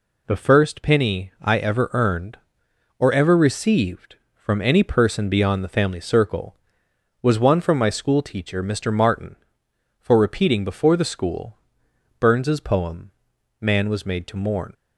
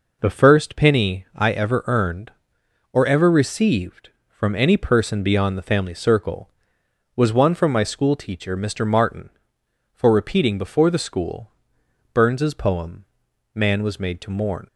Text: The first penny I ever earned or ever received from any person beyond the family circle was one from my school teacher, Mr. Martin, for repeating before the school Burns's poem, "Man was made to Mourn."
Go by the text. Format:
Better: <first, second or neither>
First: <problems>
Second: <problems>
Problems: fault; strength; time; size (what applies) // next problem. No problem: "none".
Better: first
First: pauses between "school" and "Burns's"; noticeable; at 11.5 s; 0.62 s long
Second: starts louder than the rest; noticeable; until 1.4 s; 5 dB // pauses between "school" and "Burns's"; noticeable; at 11.5 s; 0.62 s long